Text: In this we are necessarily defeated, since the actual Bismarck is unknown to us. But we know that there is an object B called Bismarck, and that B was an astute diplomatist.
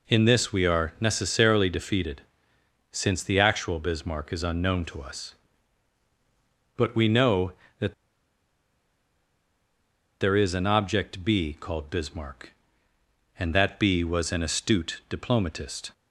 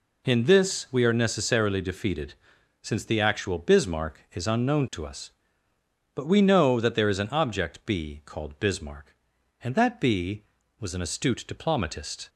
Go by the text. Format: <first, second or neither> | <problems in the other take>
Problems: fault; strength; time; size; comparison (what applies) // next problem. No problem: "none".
second | pauses between "that" and "there"; strong; at 7.9 s; 2.2 s long